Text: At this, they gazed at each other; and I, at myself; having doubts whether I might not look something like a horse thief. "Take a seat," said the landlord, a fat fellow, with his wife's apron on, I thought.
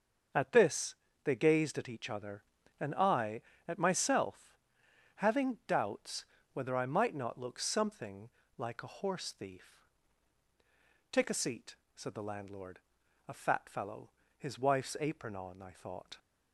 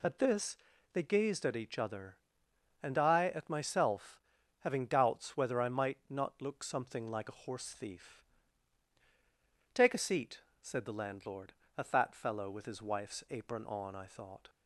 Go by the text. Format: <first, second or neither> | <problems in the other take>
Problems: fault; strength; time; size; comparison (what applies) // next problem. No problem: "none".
second | starts louder than the rest; until 1.6 s; 6.5 dB // pauses between "doubts" and "whether"; slight; at 6.2 s; 0.28 s long // pauses between "something" and "like"; slight; at 8.2 s; 0.28 s long // skips "with"; at 14.2 s